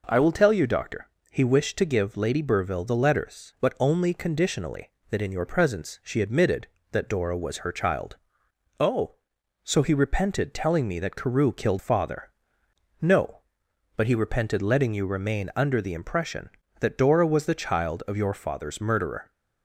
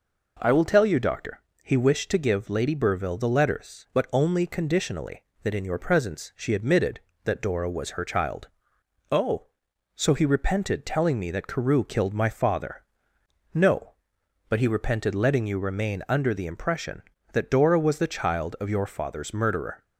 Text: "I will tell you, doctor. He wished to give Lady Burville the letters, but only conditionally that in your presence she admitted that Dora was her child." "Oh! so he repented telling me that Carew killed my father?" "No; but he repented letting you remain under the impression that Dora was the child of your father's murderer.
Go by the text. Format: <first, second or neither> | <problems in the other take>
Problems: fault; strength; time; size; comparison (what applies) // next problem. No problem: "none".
second | skips "my"; at 11.7 s